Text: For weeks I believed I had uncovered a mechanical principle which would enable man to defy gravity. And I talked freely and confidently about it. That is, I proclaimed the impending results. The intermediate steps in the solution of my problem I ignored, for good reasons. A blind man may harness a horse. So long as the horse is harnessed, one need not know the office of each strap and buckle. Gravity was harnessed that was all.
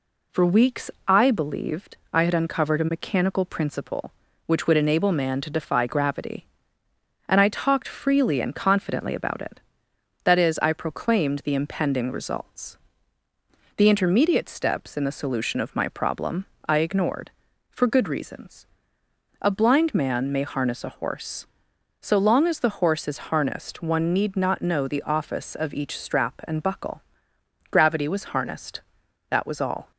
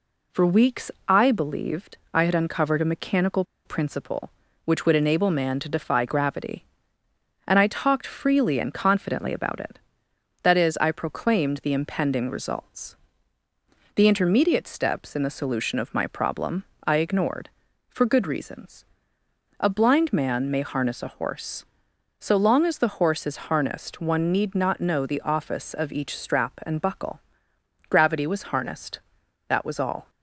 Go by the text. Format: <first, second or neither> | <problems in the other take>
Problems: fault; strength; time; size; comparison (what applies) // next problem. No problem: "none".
first | pauses between "weeks" and "I"; slight; at 0.9 s; 0.16 s long; slight in the first // pauses between "believed" and "I"; slight; at 1.9 s; 0.18 s long; slight in the first // pauses between "mechanical" and "principle"; slight; at 3.4 s; 0.20 s long // pauses between "problem" and "I"; slight; at 16.6 s; 0.22 s long; slight in the first